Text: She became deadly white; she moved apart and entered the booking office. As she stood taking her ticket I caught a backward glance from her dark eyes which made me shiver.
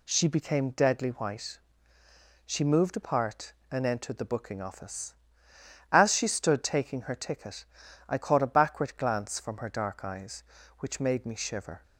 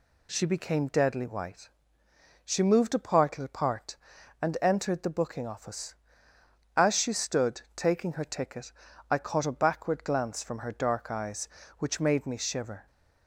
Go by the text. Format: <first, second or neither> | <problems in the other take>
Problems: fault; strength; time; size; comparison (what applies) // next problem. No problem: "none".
first | says "apart" twice; at 3.3 s // pauses between "ticket" and "I"; at 8.6 s; 0.40 s long; also in the first